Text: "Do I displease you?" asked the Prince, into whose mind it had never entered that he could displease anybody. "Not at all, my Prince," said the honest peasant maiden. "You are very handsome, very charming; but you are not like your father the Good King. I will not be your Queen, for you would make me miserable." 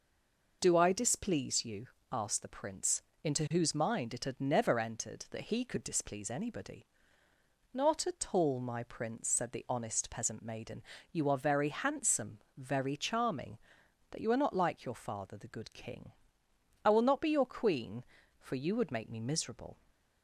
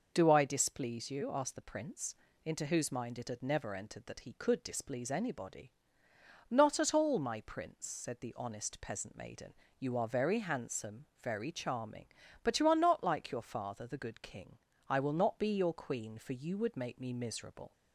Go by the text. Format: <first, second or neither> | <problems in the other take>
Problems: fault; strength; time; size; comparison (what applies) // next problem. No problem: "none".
second | stays silent before the first word; slight; until 0.6 s; 0.6 s long